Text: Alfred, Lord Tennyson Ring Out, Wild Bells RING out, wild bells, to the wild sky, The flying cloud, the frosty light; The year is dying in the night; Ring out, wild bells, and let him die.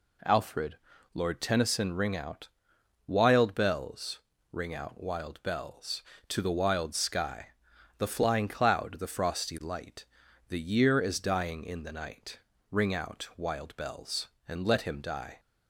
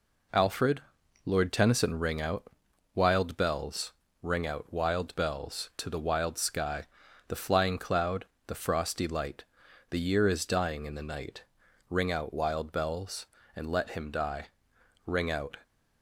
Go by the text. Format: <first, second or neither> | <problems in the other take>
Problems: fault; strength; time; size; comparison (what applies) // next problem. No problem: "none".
first | pauses between "Bells" and "RING"; slight; at 3.9 s; 0.28 s long; slight in the first // goes on to say "Ring out"; from 15.0 s on; 0.52 s long